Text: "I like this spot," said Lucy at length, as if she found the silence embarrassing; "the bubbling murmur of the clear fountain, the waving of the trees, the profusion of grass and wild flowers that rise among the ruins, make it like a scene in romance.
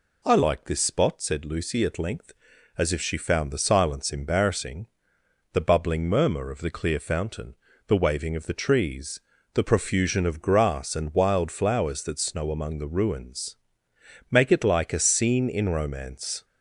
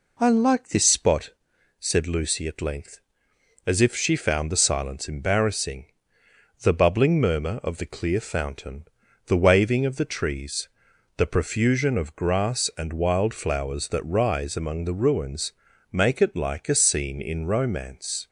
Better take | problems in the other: second | says "snow" for "rise"; at 12.1 s

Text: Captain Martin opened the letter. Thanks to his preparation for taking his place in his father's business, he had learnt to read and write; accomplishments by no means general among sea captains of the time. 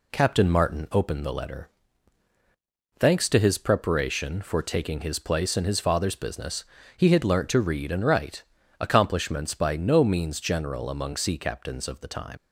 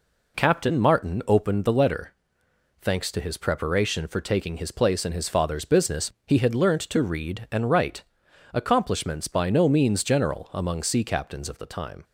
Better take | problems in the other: second | leaves "time" unfinished; at 12.3 s; 90 ms

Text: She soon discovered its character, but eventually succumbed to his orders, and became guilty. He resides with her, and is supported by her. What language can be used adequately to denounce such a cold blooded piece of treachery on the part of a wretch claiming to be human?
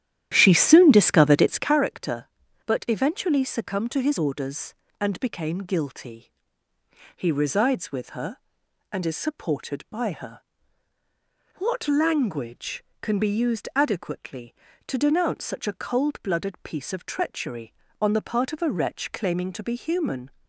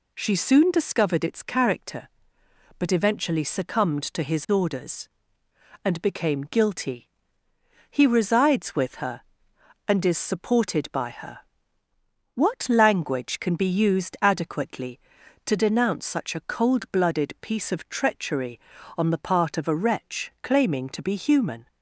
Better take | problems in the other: second | starts louder than the rest; strong; until 1.8 s; 12 dB

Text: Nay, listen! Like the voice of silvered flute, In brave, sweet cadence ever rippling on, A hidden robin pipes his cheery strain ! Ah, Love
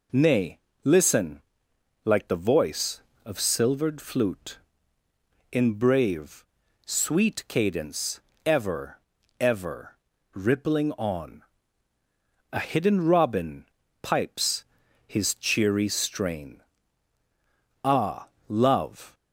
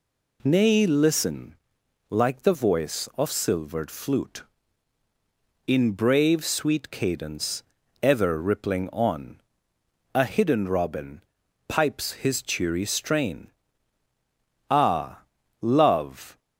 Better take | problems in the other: second | pauses between "cadence" and "ever"; slight; at 8.1 s; 0.26 s long; slight in the second // says "ever" twice; at 9.3 s // pauses between "robin" and "pipes"; slight; at 13.6 s; 0.36 s long; also in the second // pauses between "pipes" and "his"; at 14.6 s; 0.42 s long

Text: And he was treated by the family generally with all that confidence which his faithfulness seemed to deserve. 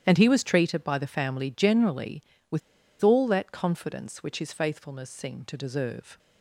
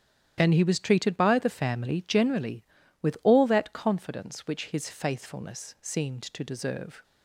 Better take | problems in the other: second | starts louder than the rest; strong; until 1.0 s; 10.5 dB; strong in the second // pauses between "with" and "all"; at 2.6 s; 0.41 s long

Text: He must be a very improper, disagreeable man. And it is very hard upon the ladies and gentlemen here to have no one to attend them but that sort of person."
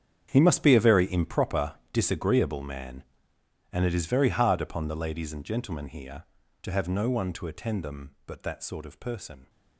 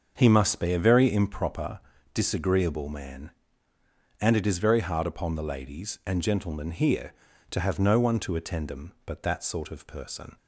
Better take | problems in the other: second | gets quieter; strong; throughout; 16 dB // starts louder than the rest; strong; until 1.3 s; 8.5 dB; also in the second

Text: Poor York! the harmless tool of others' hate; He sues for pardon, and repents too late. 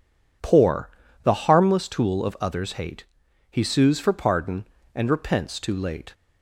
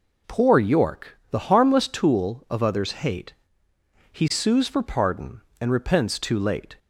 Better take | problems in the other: second | skips "York"; at 1.0 s

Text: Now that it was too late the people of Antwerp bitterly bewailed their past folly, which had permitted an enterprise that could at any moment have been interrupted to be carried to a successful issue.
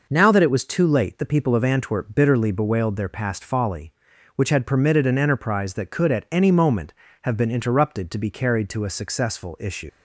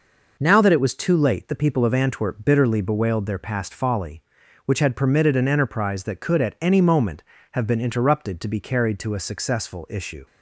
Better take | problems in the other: second | leaves "issue" unfinished; at 9.8 s; 60 ms

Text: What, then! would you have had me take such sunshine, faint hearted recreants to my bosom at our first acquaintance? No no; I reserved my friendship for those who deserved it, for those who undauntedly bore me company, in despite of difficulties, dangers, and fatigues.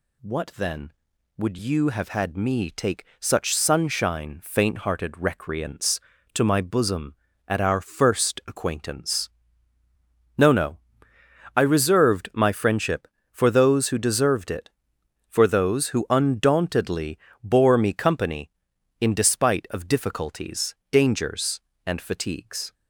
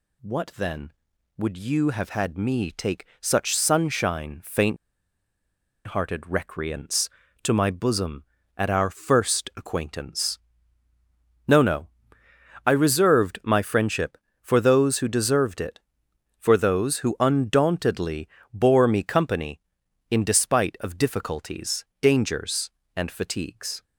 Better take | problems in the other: first | pauses between "take" and "such"; slight; at 3.0 s; 0.16 s long; slight in the first // pauses between "faint" and "hearted"; at 4.7 s; 1.1 s long // pauses between "undauntedly" and "bore"; slight; at 18.2 s; 0.24 s long; slight in the first

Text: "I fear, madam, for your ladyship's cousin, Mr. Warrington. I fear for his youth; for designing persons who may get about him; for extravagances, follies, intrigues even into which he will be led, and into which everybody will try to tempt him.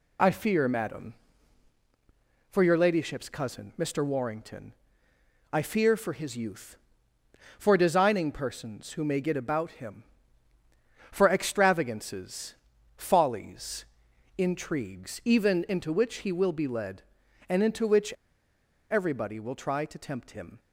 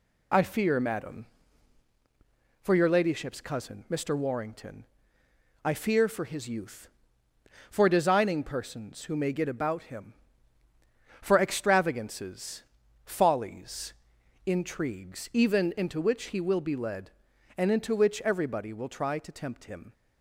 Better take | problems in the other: second | pauses between "which" and "everybody"; noticeable; at 18.1 s; 0.77 s long

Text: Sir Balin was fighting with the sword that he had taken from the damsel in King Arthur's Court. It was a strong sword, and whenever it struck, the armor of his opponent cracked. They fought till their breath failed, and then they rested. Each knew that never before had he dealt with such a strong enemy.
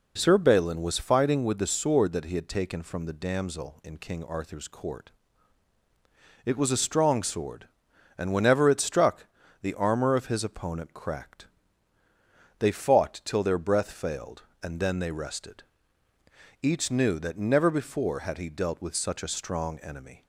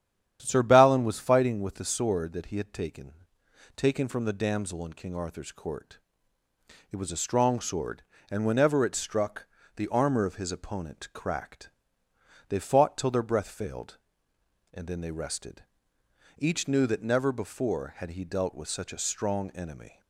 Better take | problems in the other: first | starts louder than the rest; strong; until 1.4 s; 10 dB // says "taken" twice; at 3.7 s

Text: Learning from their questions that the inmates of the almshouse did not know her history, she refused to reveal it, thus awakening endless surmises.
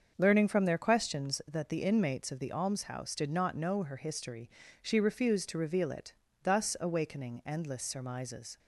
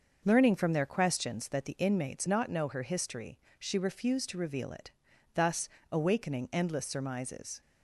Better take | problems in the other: first | starts louder than the rest; noticeable; until 1.2 s; 6 dB; also in the first // skips "of the almshouse did"; at 2.2 s // pauses between "thus" and "awakening"; slight; at 5.6 s; 0.24 s long

